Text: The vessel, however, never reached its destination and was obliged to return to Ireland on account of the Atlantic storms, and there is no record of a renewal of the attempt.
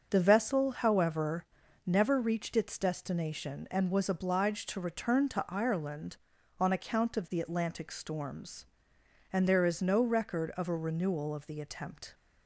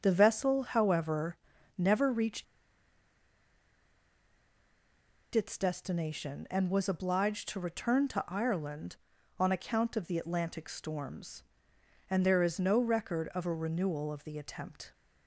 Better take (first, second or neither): first